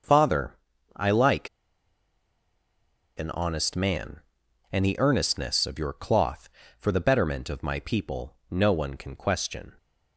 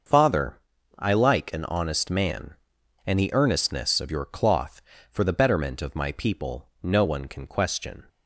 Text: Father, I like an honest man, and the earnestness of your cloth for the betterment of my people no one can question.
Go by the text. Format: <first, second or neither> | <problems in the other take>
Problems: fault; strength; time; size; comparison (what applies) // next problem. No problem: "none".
second | starts louder than the rest; until 1.4 s; 6.5 dB; also in the second // pauses between "like" and "an"; strong; at 1.4 s; 1.6 s long // pauses between "people" and "no"; slight; at 8.3 s; 0.16 s long; slight in the second